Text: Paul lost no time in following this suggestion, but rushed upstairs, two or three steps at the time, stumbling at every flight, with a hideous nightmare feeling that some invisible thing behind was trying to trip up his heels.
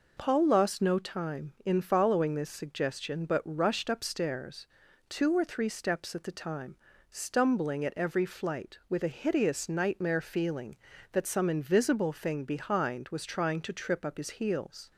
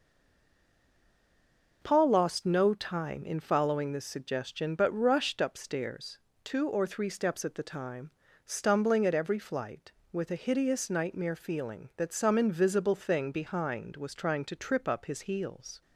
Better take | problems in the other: first | stays silent before the first word; noticeable; until 1.8 s; 1.8 s long

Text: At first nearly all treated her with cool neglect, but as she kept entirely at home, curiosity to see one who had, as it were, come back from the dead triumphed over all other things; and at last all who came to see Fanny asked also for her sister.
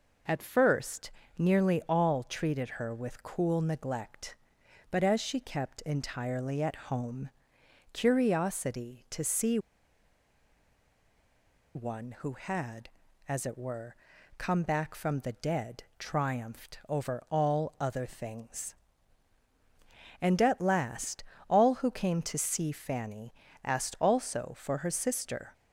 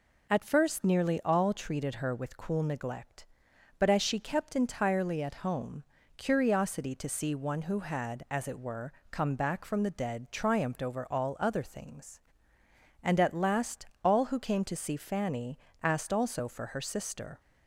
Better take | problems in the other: second | pauses between "first" and "nearly"; slight; at 1.1 s; 0.28 s long // pauses between "see" and "one"; strong; at 9.5 s; 2.1 s long // pauses between "dead" and "triumphed"; slight; at 15.8 s; 0.16 s long // pauses between "last" and "all"; slight; at 21.2 s; 0.24 s long; slight in the second // pauses between "Fanny" and "asked"; slight; at 23.3 s; 0.28 s long; slight in the second

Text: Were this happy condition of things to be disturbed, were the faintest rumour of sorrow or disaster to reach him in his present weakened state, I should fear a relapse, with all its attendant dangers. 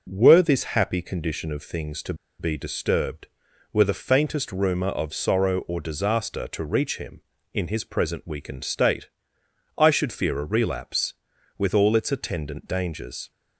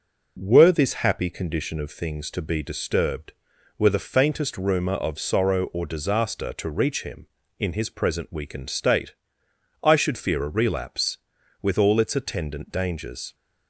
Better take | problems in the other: second | pauses between "to" and "be"; slight; at 2.1 s; 0.25 s long

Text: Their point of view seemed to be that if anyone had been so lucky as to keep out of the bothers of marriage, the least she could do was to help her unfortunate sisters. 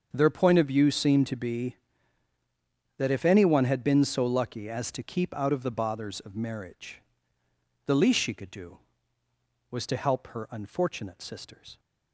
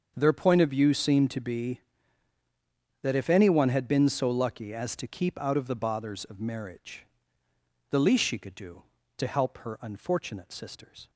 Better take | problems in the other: first | starts louder than the rest; until 1.1 s; 6.5 dB; also in the first // skips "was"; at 9.0 s

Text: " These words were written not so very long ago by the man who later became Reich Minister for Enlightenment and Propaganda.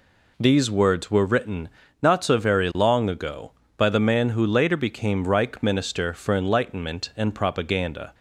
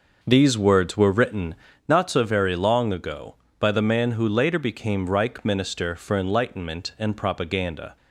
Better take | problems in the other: first | starts louder than the rest; noticeable; until 2.0 s; 5.5 dB // pauses between "written" and "not"; slight; at 1.5 s; 0.32 s long; slight in the first

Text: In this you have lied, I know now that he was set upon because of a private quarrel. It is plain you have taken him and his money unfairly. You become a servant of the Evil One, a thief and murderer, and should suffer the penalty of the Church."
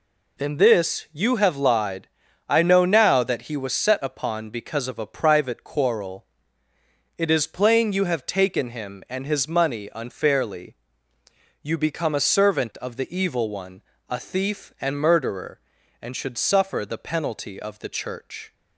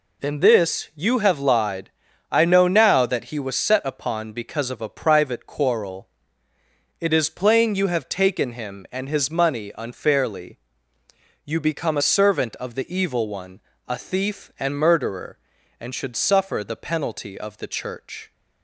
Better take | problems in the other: neither | none

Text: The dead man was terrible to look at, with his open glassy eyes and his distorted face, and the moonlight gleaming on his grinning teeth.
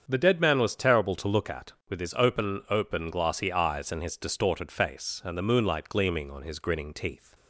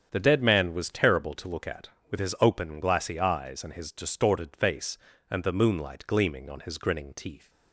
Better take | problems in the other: second | starts louder than the rest; strong; until 1.0 s; 7.5 dB; strong in the second // says "open" twice; at 2.6 s

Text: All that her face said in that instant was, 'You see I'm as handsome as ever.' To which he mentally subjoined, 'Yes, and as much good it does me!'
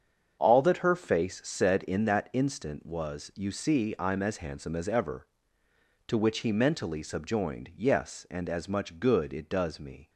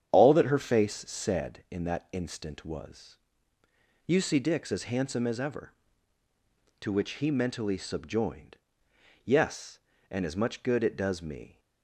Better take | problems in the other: first | starts louder than the rest; strong; until 1.1 s; 8.5 dB; strong in the first // says "Dix" for "I'm"; at 4.3 s

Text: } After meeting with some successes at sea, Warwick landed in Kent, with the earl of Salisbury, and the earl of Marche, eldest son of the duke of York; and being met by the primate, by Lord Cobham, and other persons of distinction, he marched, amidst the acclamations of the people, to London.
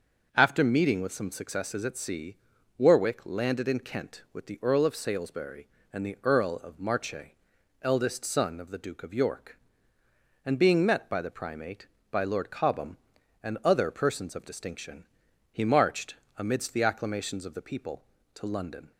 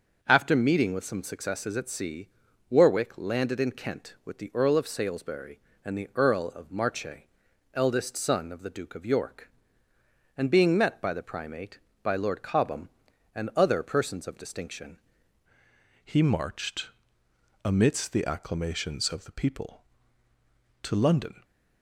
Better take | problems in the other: first | starts louder than the rest; until 1.2 s; 6 dB; also in the first // changes voice at "he"; from 16.0 s on; 5.4 s long

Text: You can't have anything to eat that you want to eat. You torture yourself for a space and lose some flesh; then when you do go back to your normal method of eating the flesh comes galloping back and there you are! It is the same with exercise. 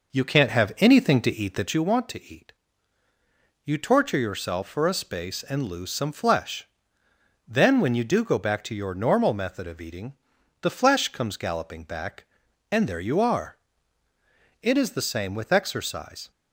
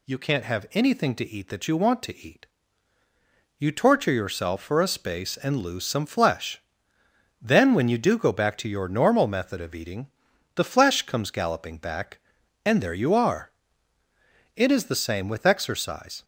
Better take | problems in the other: second | starts louder than the rest; noticeable; until 1.8 s; 5.5 dB // pauses between "eating" and "the"; noticeable; at 10.1 s; 0.48 s long; noticeable in the second

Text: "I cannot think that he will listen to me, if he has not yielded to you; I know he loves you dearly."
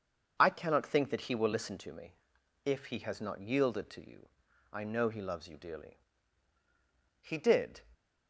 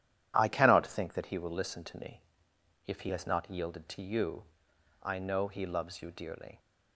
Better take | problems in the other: second | goes on to say "He did"; from 7.2 s on; 0.60 s long

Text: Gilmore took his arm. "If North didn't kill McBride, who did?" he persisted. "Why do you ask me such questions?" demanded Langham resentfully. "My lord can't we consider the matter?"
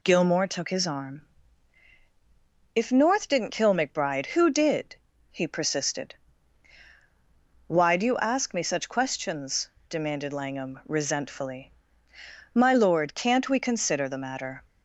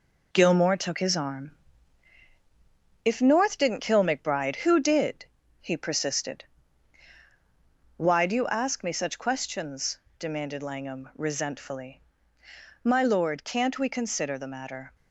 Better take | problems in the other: first | gets quieter; noticeable; throughout; 6 dB

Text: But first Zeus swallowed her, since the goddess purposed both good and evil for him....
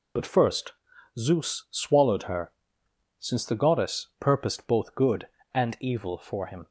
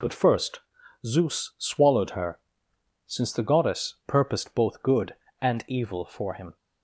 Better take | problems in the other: second | loses the start of "But"; at 0.1 s; 20 ms // pauses between "first" and "Zeus"; at 0.7 s; 0.44 s long; also in the second

